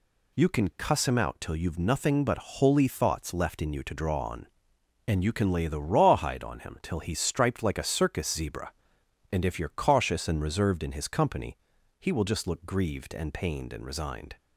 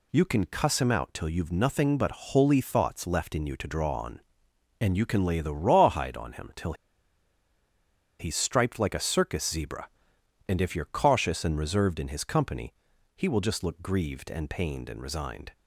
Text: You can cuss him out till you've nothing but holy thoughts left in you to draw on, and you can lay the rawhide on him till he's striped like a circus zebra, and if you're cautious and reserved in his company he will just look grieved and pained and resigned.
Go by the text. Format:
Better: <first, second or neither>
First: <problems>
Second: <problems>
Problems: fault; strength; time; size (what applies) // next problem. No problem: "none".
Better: first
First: pauses between "company" and "he"; at 11.5 s; 0.42 s long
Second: pauses between "till" and "he's"; strong; at 6.7 s; 1.4 s long // pauses between "company" and "he"; at 12.7 s; 0.42 s long